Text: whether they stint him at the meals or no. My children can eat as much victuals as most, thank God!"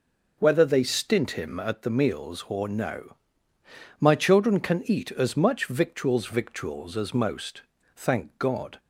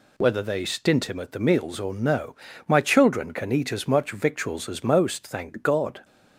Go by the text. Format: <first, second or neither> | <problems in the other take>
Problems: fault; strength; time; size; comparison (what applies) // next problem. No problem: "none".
second | says "victuals" twice; at 6.2 s